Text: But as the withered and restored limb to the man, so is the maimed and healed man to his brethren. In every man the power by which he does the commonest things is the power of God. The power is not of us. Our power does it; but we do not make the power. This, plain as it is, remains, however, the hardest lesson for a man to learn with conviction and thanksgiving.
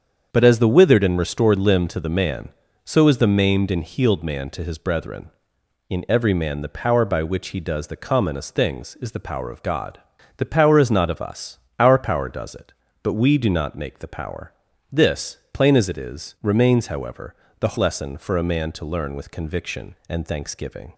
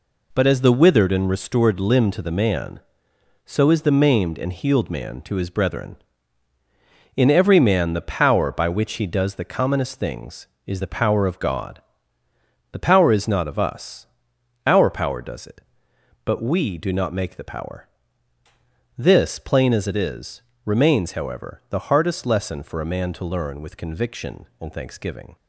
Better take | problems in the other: second | starts louder than the rest; strong; until 1.3 s; 7.5 dB // skips "hardest"; at 17.7 s

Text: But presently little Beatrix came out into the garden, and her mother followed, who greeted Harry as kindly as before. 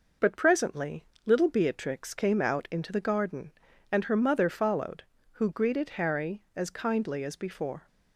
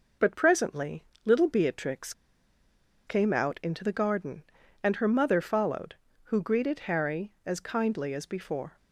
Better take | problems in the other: first | pauses between "presently" and "little"; slight; at 1.0 s; 0.22 s long; slight in the first // pauses between "Beatrix" and "came"; noticeable; at 2.1 s; 0.94 s long

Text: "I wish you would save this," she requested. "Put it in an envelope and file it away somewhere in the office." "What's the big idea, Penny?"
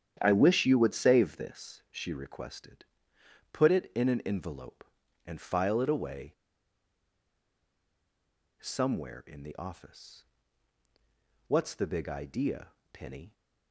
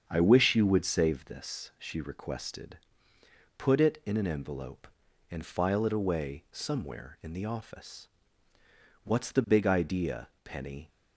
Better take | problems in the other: second | starts louder than the rest; strong; until 1.2 s; 9.5 dB; strong in the second // pauses between "away" and "somewhere"; strong; at 6.3 s; 2.2 s long

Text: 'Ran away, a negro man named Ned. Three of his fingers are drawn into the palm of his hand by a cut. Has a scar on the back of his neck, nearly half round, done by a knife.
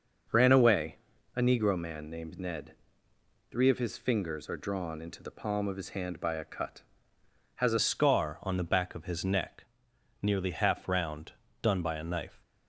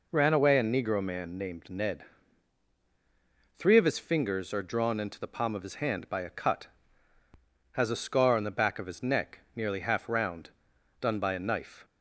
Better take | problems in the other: second | starts louder than the rest; until 1.7 s; 6 dB // changes voice at "scar"; from 7.7 s on; 4.7 s long

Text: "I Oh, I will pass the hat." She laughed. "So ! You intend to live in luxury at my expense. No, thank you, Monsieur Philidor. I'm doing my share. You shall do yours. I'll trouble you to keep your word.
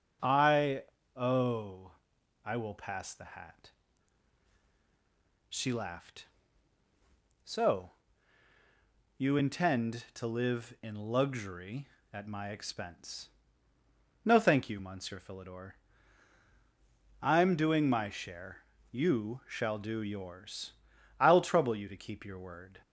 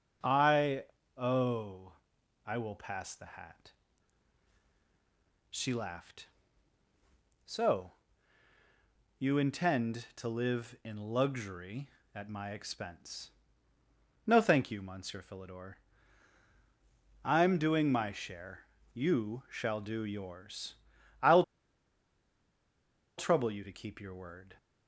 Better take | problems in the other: first | pauses between "I" and "Oh"; slight; at 0.8 s; 0.34 s long; slight in the first // pauses between "I'll" and "trouble"; strong; at 21.4 s; 1.7 s long

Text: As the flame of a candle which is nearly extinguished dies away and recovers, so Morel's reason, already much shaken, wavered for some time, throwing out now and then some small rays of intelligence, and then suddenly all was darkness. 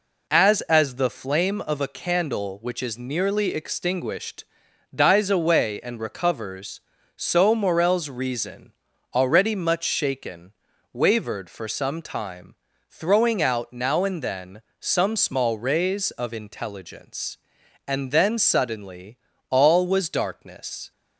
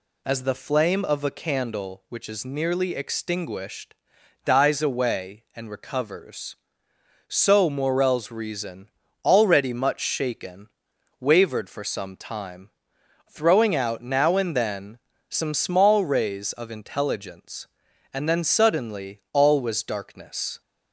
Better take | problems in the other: second | says "As" twice; at 0.6 s // pauses between "extinguished" and "dies"; noticeable; at 4.4 s; 0.50 s long; noticeable in the second // pauses between "then" and "some"; slight; at 14.6 s; 0.20 s long; slight in the second // pauses between "suddenly" and "all"; slight; at 19.1 s; 0.32 s long

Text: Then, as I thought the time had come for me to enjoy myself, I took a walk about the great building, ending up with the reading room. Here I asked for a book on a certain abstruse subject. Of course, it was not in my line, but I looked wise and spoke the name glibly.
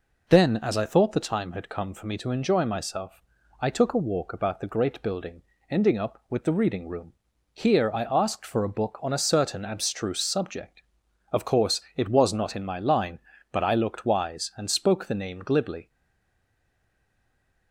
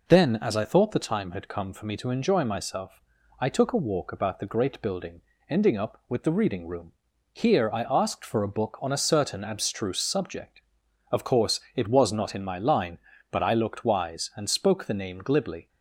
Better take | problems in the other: second | stays silent after the last word; noticeable; from 15.8 s on; 1.9 s long

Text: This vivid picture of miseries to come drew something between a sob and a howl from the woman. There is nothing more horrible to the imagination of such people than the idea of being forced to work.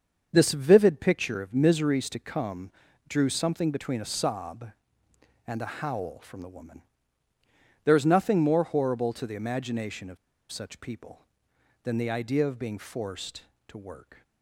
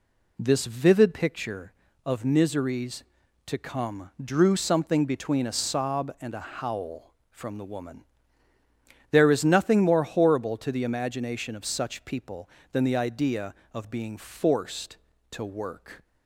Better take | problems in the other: second | starts louder than the rest; until 1.3 s; 7 dB // pauses between "come" and "drew"; at 2.7 s; 0.38 s long // pauses between "of" and "such"; slight; at 10.1 s; 0.34 s long

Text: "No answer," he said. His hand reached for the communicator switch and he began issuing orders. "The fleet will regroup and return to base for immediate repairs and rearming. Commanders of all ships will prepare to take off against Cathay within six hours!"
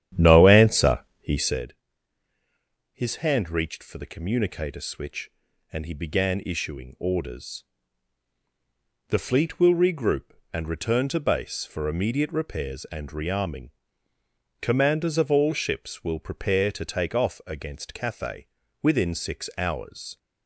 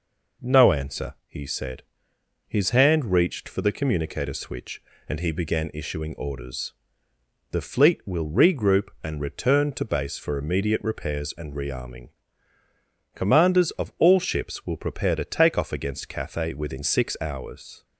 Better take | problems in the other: second | starts louder than the rest; strong; until 1.7 s; 10.5 dB // pauses between "Cathay" and "within"; at 18.4 s; 0.36 s long

